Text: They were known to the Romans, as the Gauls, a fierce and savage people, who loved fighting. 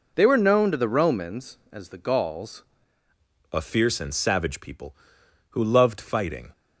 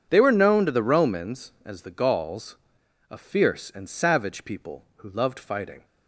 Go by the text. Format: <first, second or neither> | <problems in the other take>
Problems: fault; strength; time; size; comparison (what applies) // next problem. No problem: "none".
second | changes voice at "a"; from 3.5 s on; 3.0 s long